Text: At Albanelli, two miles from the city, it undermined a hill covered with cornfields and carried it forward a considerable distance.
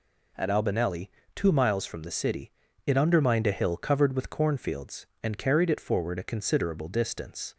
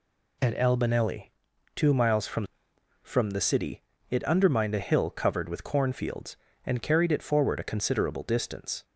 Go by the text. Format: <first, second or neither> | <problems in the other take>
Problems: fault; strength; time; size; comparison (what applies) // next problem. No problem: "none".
first | says "from" twice; at 3.0 s